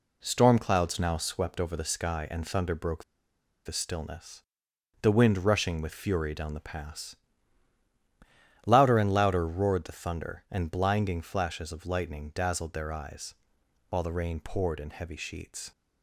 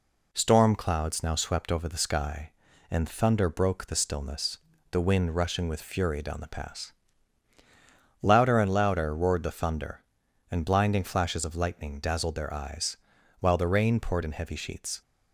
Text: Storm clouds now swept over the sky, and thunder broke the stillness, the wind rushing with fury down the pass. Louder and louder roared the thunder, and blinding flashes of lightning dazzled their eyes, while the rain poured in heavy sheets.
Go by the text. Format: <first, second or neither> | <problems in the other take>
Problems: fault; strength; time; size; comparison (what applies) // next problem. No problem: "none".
second | pauses between "broke" and "the"; noticeable; at 3.0 s; 0.62 s long